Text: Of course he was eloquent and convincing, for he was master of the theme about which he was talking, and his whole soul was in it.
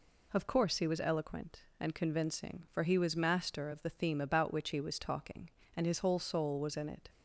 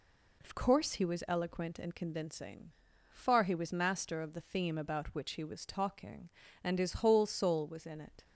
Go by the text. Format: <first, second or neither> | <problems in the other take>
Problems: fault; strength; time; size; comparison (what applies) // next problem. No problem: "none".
first | says "far" for "for"; at 3.1 s